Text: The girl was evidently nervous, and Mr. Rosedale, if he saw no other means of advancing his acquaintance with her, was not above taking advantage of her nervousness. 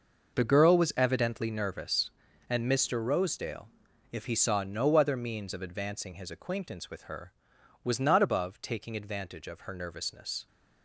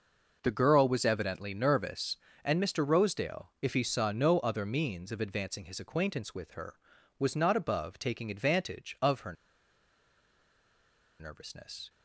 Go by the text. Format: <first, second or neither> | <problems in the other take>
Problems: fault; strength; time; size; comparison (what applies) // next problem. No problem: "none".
first | pauses between "her" and "nervousness"; strong; at 9.3 s; 1.8 s long